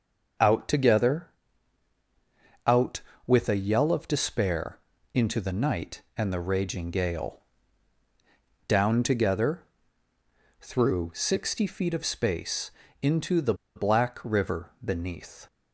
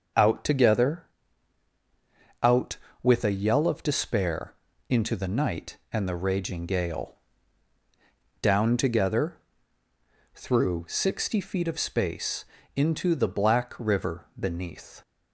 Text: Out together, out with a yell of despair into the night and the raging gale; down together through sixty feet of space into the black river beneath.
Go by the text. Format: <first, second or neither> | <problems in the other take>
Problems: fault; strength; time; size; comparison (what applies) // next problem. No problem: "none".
second | starts louder than the rest; until 2.8 s; 7 dB; also in the second // pauses between "despair" and "into"; slight; at 4.7 s; 0.34 s long; slight in the second // pauses between "together" and "through"; noticeable; at 9.6 s; 0.96 s long; noticeable in the second // pauses between "space" and "into"; slight; at 12.6 s; 0.32 s long; slight in the second // pauses between "the" and "black"; slight; at 13.5 s; 0.22 s long